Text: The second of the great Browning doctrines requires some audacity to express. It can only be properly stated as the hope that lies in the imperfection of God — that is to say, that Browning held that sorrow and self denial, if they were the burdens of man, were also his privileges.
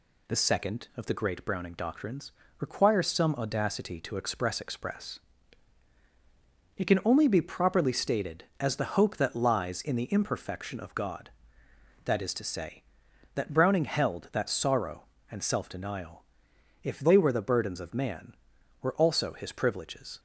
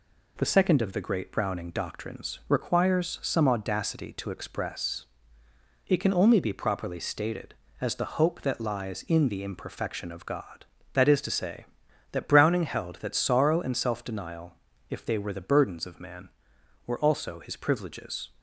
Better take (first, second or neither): second